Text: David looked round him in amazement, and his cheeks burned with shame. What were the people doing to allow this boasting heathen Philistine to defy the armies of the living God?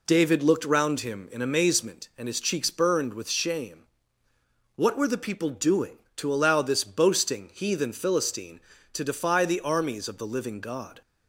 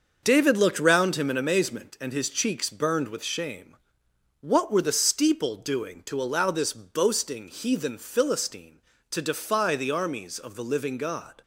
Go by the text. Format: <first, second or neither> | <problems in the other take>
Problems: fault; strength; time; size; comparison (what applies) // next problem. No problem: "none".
first | starts louder than the rest; until 1.2 s; 6 dB // says "steeple" for "people"; at 4.9 s